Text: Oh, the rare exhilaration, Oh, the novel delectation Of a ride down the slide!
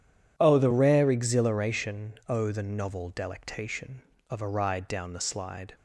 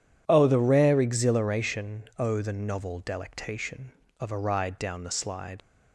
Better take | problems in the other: first | leaves "slide" unfinished; at 5.6 s; 55 ms

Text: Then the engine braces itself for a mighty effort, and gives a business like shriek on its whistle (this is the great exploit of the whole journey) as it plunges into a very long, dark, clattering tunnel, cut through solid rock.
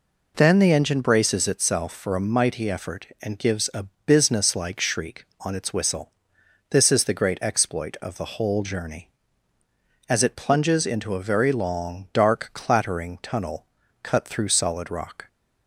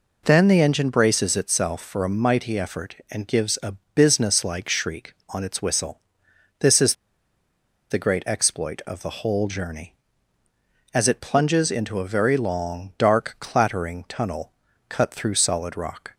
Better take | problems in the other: first | pauses between "a" and "business"; slight; at 3.7 s; 0.20 s long; slight in the first // pauses between "is" and "the"; noticeable; at 6.9 s; 0.96 s long

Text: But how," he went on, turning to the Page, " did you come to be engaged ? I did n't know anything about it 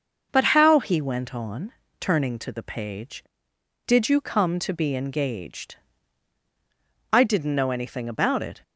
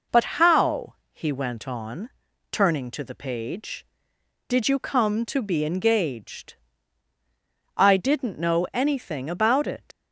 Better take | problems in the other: first | leaves "it" unfinished; at 9.9 s; 120 ms

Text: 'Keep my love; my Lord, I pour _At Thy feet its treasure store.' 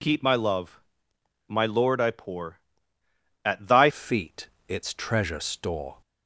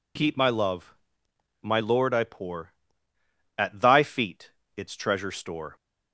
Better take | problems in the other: second | changes voice at "feet"; from 3.9 s on; 2.0 s long // pauses between "feet" and "its"; slight; at 4.4 s; 0.20 s long; slight in the second

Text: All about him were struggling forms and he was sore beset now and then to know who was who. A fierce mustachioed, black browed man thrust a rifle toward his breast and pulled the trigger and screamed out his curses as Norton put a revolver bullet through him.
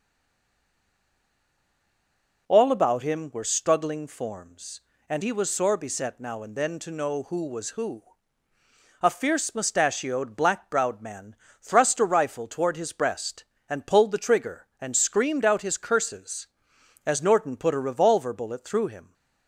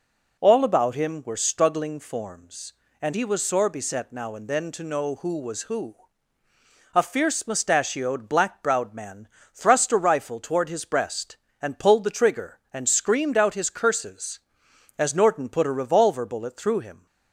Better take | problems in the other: second | stays silent before the first word; until 2.4 s; 2.4 s long // pauses between "man" and "thrust"; slight; at 11.3 s; 0.26 s long; slight in the second

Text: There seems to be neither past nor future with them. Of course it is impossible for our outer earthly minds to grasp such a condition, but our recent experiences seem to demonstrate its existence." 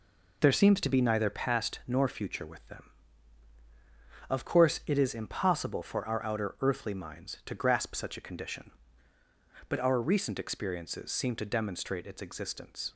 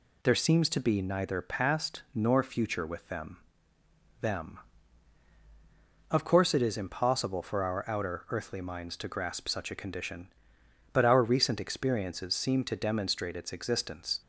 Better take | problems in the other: first | says "them" twice; at 4.2 s

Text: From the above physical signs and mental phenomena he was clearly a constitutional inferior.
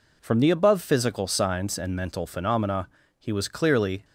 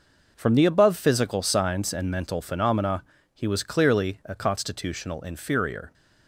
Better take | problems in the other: second | pauses between "phenomena" and "he"; slight; at 2.8 s; 0.30 s long; slight in the second // stops before "a constitutional inferior"; at 4.0 s

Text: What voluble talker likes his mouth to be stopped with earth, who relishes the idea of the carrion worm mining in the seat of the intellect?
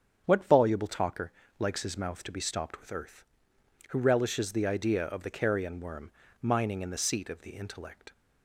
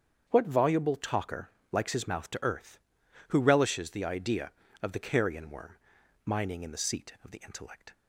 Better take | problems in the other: first | starts louder than the rest; strong; until 1.2 s; 7.5 dB; strong in the first // pauses between "talker" and "likes"; slight; at 1.5 s; 0.20 s long; slight in the first // skips "be stopped with"; at 2.4 s // pauses between "worm" and "mining"; noticeable; at 5.7 s; 0.48 s long; slight in the first

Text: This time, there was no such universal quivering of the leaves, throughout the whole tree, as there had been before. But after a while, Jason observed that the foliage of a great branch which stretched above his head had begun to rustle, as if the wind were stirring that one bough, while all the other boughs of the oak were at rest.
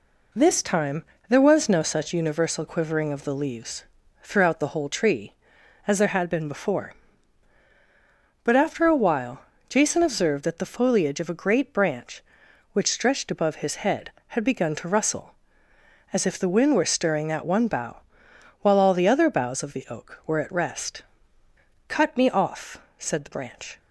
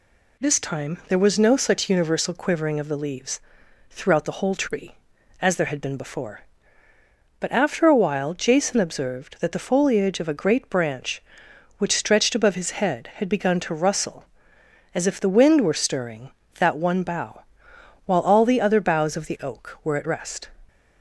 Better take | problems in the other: second | goes on to say "Cut me off said the branch"; strong; from 21.8 s on; 1.9 s long

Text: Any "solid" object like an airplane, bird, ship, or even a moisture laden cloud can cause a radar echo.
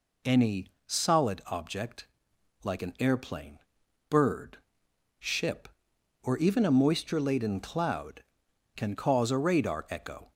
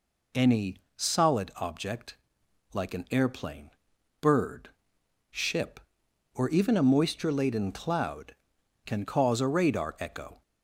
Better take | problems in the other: neither | pauses between "Any" and "solid"; slight; the same in both // pauses between "object" and "like"; noticeable; the same in both

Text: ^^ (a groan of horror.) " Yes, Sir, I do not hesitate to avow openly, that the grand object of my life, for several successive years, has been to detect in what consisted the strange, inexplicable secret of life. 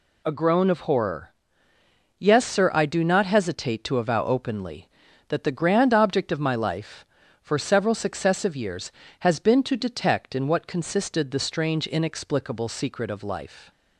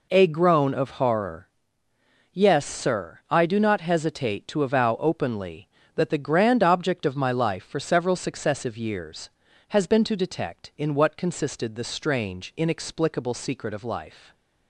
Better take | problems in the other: neither | none

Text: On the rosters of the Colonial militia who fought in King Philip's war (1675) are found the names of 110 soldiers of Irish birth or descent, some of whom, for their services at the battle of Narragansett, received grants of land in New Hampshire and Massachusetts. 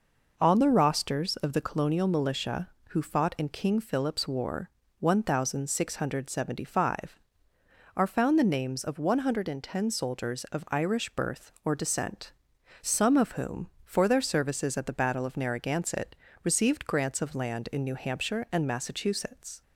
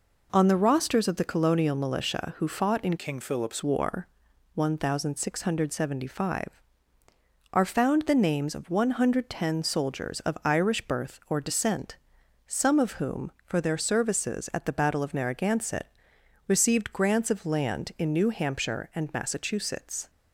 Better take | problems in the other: first | changes voice from "King" to "Philip's"; from 2.9 to 3.6 s; 0.7 s long

